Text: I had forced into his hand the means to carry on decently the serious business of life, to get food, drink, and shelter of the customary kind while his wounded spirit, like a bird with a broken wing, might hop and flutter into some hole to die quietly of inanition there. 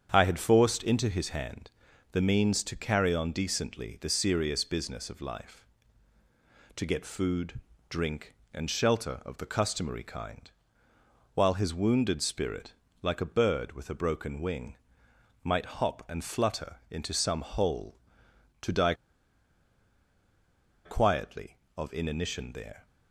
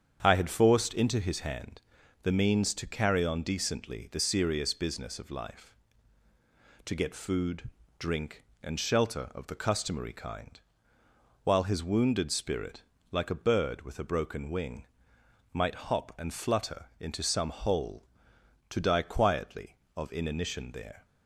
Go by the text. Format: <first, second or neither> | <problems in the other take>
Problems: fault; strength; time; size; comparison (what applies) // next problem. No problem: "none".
second | starts louder than the rest; strong; until 1.1 s; 8 dB; strong in the second // pauses between "hand" and "the"; at 1.7 s; 0.40 s long; also in the second // pauses between "kind" and "while"; noticeable; at 10.5 s; 0.84 s long; noticeable in the second // pauses between "die" and "quietly"; strong; at 18.9 s; 1.9 s long